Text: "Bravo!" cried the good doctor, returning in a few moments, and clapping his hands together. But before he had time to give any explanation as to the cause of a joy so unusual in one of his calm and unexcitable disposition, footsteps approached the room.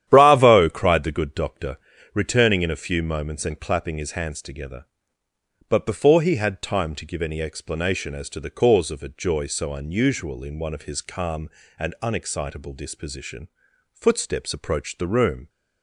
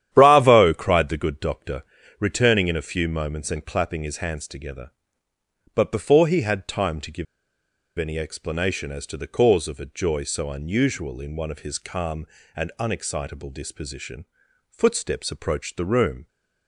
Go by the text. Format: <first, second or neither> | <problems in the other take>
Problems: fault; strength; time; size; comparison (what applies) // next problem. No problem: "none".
first | starts louder than the rest; strong; until 1.1 s; 11 dB; strong in the first // pauses between "give" and "any"; noticeable; at 7.2 s; 0.73 s long